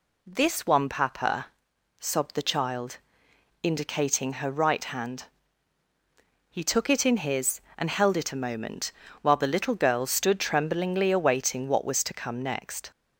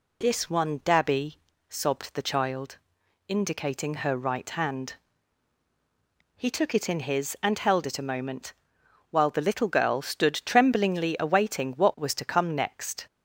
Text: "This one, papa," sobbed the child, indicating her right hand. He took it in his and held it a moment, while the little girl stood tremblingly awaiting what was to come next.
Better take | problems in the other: first | says "dabby" for "papa"; at 0.8 s

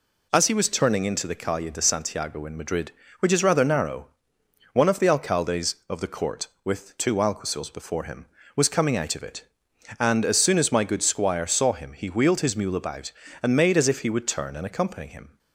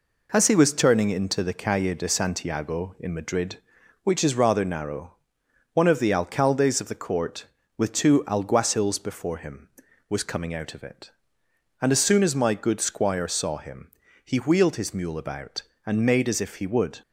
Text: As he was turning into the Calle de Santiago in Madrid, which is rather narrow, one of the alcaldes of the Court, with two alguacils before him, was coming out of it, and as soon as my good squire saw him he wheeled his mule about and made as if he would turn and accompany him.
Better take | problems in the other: first | pauses between "him" and "he"; slight; at 13.9 s; 0.34 s long // stops before "turn and accompany him"; at 17.0 s

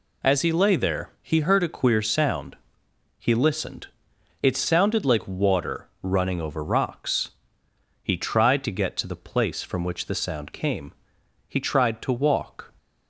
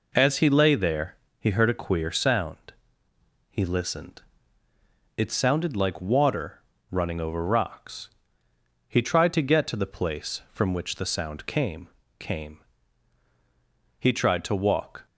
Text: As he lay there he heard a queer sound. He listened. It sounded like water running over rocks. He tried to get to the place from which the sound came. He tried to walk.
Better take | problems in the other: first | pauses between "there" and "he"; slight; at 1.1 s; 0.24 s long // pauses between "water" and "running"; slight; at 6.6 s; 0.30 s long // says "came" twice; at 12.1 s

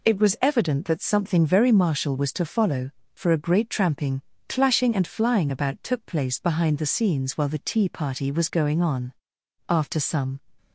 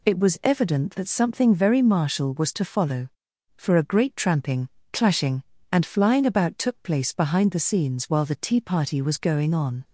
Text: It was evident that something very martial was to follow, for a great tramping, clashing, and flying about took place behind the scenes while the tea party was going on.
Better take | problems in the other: second | goes on to say "After some"; noticeable; from 9.6 s on; 0.72 s long

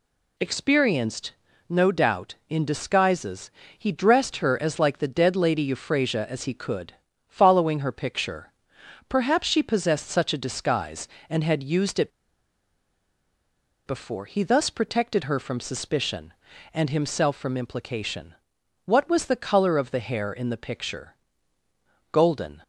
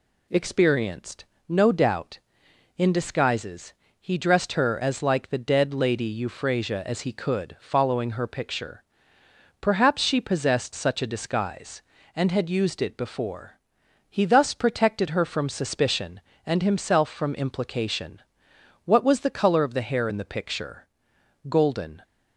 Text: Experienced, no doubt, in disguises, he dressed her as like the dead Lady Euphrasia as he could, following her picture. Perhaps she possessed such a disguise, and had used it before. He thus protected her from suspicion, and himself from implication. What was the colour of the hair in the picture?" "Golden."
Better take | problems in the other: second | pauses between "it" and "before"; strong; at 12.1 s; 1.7 s long

